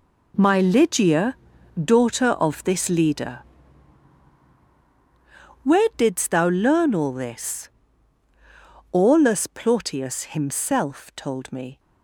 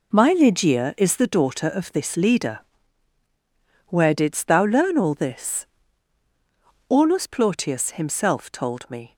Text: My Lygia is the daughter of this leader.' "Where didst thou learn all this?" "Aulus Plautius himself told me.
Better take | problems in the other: second | skips "is the"; at 1.5 s

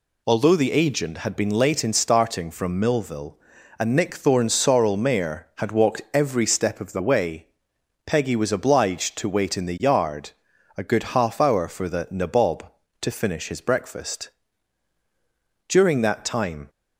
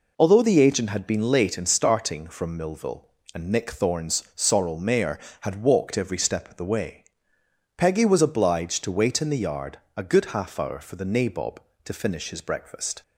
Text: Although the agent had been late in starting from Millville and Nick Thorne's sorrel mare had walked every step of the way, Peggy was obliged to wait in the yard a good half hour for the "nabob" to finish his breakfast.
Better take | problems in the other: second | pauses between "yard" and "a"; noticeable; at 10.3 s; 0.46 s long; slight in the second // goes on to say "During that time"; noticeable; from 15.6 s on; 1.0 s long

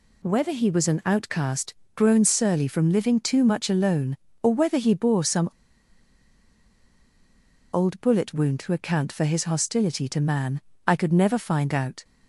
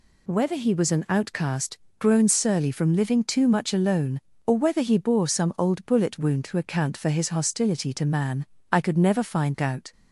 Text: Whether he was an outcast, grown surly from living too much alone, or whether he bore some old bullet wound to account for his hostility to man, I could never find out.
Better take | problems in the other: second | pauses between "some" and "old"; strong; at 5.4 s; 2.2 s long

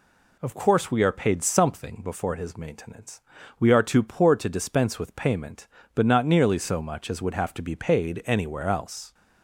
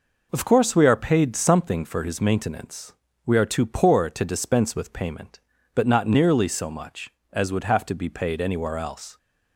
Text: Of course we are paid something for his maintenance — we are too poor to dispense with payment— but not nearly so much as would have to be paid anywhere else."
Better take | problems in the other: second | says "before" for "for"; at 2.0 s

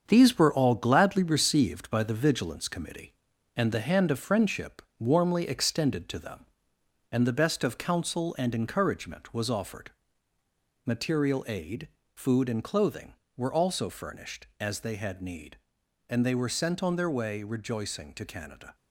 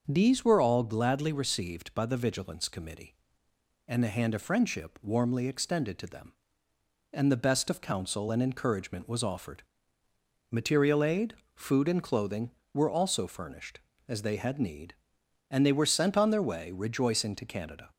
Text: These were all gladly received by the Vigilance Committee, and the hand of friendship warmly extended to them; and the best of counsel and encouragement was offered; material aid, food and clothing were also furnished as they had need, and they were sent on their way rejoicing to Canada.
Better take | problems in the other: second | gets quieter; throughout; 7 dB // starts louder than the rest; strong; until 1.0 s; 7.5 dB; also in the second // pauses between "friendship" and "warmly"; slight; at 4.8 s; 0.16 s long

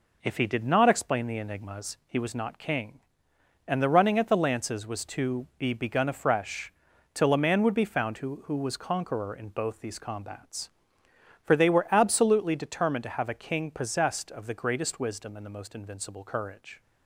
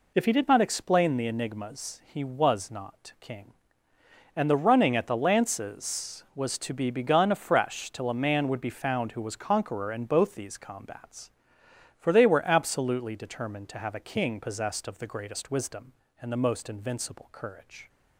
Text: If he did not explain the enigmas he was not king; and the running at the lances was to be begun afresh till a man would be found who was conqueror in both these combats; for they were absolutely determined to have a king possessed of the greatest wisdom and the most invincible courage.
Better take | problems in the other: second | pauses between "afresh" and "till"; at 6.7 s; 0.42 s long // says "who" twice; at 8.4 s

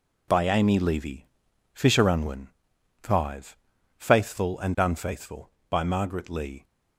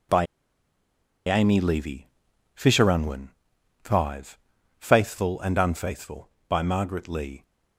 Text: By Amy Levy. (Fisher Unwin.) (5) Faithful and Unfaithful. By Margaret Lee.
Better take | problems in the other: first | pauses between "By" and "Amy"; at 0.2 s; 1.0 s long

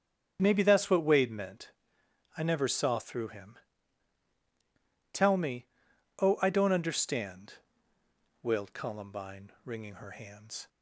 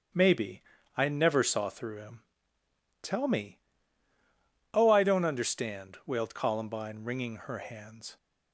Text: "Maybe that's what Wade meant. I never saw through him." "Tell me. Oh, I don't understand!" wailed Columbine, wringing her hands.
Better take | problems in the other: first | starts louder than the rest; strong; until 1.4 s; 8.5 dB; strong in the first // skips "that's what Wade meant"; at 0.7 s

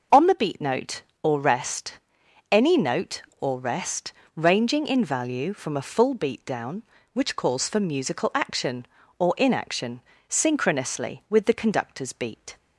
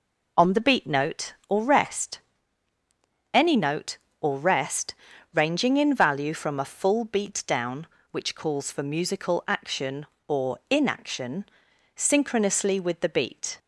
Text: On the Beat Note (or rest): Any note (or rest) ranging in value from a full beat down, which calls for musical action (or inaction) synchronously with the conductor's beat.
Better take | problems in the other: first | skips "conductor's"; at 13.0 s

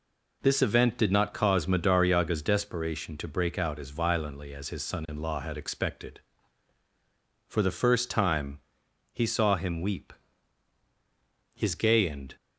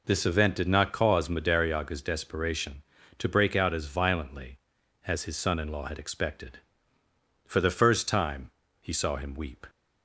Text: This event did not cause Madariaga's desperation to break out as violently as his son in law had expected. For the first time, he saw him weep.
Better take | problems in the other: second | goes on to say "His gay and"; noticeable; from 11.5 s on; 0.80 s long

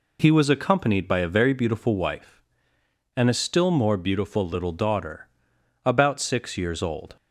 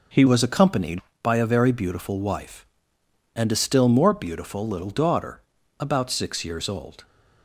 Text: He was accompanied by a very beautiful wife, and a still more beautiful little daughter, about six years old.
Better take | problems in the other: first | changes voice at "was"; from 0.2 s on; 6.8 s long

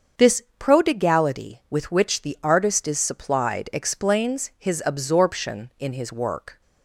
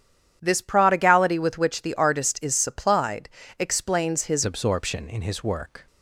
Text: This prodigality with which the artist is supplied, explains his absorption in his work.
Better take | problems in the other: first | starts louder than the rest; strong; until 1.4 s; 9.5 dB; also in the first // changes voice at "absorption"; from 4.4 s on; 1.4 s long

